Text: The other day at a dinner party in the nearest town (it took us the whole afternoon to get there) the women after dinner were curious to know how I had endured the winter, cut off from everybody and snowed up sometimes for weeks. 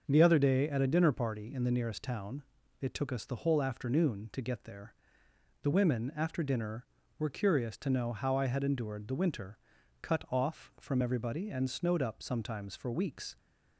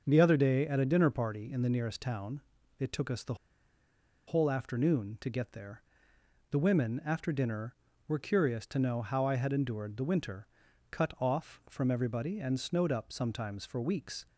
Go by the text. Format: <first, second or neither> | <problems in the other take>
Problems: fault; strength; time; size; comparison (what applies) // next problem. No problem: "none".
first | starts louder than the rest; until 1.0 s; 6 dB; also in the first // pauses between "the" and "whole"; noticeable; at 3.3 s; 0.92 s long